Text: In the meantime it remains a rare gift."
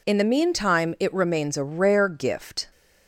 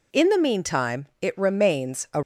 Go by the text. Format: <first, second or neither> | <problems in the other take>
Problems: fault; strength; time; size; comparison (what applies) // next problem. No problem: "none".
first | stops before "rare gift"; at 2.2 s